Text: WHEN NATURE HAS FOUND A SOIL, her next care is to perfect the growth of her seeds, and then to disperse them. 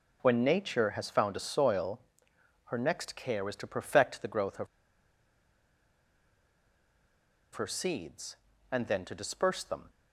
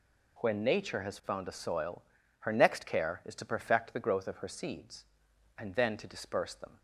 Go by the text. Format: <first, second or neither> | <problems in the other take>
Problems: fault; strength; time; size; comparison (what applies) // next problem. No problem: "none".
second | pauses between "of" and "her"; strong; at 4.6 s; 2.8 s long